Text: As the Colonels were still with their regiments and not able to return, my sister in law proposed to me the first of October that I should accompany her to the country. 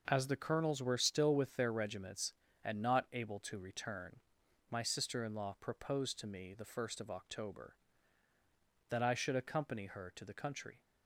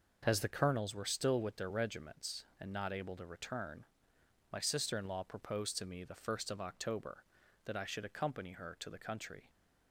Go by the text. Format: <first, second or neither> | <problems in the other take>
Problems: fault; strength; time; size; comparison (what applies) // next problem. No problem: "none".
neither | none